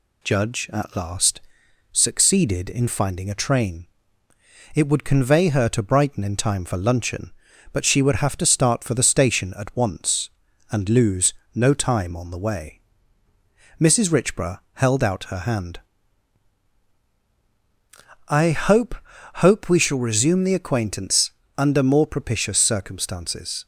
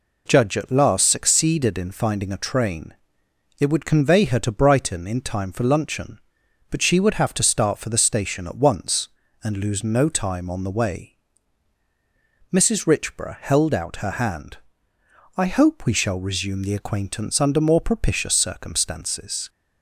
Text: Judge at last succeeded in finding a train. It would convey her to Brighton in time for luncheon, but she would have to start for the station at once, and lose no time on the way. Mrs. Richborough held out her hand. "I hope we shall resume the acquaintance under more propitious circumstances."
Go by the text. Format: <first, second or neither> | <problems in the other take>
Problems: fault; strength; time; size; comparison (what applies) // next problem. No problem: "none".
second | pauses between "last" and "succeeded"; noticeable; at 1.3 s; 0.52 s long // pauses between "lose" and "no"; slight; at 11.3 s; 0.20 s long // says "hope" twice; at 19.3 s // pauses between "acquaintance" and "under"; slight; at 21.3 s; 0.26 s long